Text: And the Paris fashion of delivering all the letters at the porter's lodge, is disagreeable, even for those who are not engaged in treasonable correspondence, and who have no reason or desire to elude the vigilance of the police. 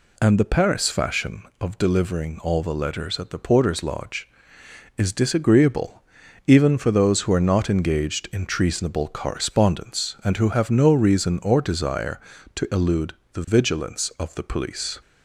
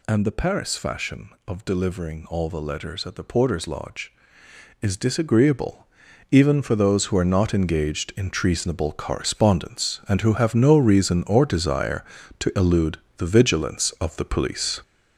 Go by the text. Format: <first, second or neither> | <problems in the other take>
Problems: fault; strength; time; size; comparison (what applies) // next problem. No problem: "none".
first | gets louder; strong; throughout; 7.5 dB // pauses between "elude" and "the"; slight; at 12.9 s; 0.22 s long; slight in the first